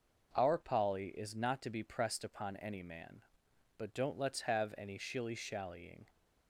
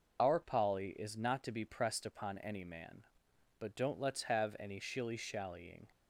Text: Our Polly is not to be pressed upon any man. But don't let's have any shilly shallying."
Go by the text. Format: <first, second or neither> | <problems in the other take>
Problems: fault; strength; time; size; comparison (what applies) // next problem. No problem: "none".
first | loses the start of "Our"; at 0.1 s; 65 ms